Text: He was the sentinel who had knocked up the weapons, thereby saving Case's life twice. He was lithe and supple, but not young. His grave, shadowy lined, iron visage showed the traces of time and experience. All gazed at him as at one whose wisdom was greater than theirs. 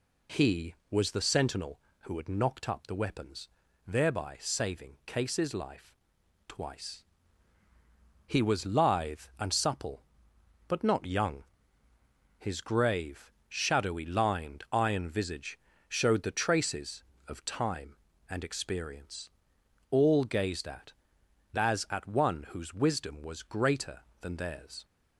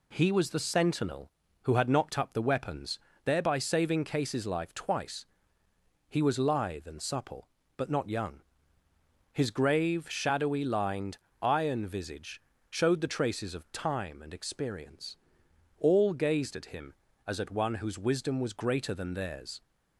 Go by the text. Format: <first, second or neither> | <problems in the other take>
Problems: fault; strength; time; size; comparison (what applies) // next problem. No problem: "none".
second | pauses between "life" and "twice"; noticeable; at 5.9 s; 0.54 s long // pauses between "visage" and "showed"; slight; at 15.5 s; 0.30 s long; slight in the second // skips "him"; at 21.2 s